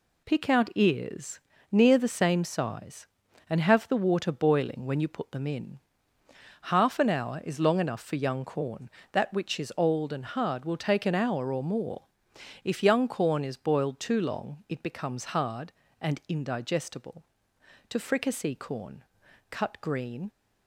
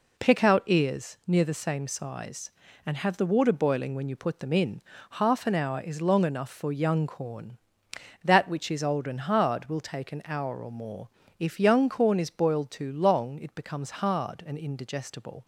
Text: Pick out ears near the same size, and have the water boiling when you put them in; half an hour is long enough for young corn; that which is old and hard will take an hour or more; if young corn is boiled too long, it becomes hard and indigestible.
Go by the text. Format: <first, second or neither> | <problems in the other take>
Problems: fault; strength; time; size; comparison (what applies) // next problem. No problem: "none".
second | pauses between "ears" and "near"; slight; at 1.3 s; 0.32 s long // goes on to say "To Fricassee Corn Cut green"; strong; from 17.8 s on; 2.4 s long